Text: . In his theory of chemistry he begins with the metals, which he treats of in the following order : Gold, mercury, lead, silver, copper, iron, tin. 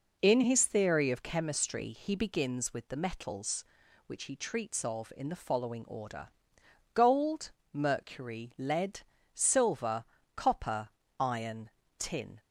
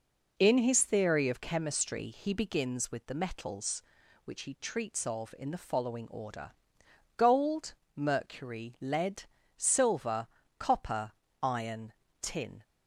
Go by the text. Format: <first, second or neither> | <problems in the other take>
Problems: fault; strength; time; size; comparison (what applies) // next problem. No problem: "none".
neither | none